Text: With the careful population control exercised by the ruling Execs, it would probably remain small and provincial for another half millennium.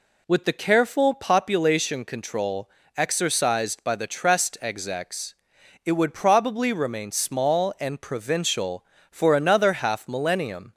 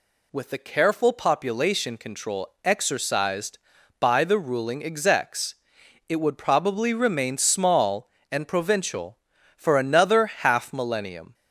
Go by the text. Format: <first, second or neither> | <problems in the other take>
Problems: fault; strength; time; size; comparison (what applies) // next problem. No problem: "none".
second | pauses between "control" and "exercised"; slight; at 2.7 s; 0.26 s long // says "trest" for "ruling"; at 4.0 s